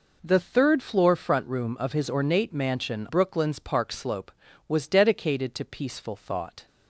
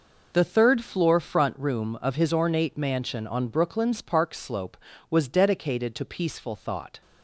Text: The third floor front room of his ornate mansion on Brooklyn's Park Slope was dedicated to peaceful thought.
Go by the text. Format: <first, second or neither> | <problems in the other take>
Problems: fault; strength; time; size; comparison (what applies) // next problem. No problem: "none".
second | skips "on"; at 3.0 s